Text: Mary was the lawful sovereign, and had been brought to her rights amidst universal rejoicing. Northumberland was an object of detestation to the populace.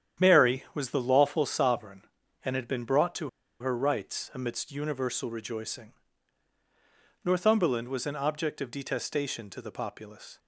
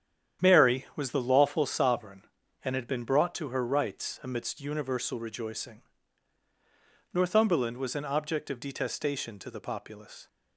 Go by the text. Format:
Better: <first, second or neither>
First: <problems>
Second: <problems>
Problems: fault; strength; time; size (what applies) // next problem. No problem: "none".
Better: second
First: starts louder than the rest; strong; until 1.3 s; 9.5 dB // pauses between "to" and "her"; slight; at 3.2 s; 0.30 s long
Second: starts louder than the rest; strong; until 1.5 s; 9.5 dB